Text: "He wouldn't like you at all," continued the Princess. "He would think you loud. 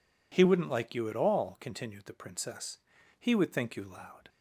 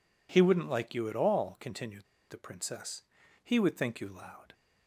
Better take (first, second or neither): first